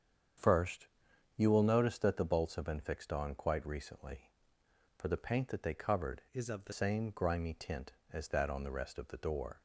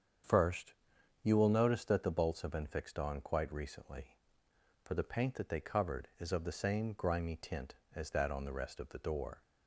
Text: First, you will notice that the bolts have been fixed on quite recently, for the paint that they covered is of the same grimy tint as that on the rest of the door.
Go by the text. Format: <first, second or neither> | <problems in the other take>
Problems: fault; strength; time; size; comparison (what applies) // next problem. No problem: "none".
second | starts louder than the rest; strong; until 1.8 s; 8 dB; strong in the second // changes voice from "is" to "the"; from 6.3 to 6.7 s; 0.4 s long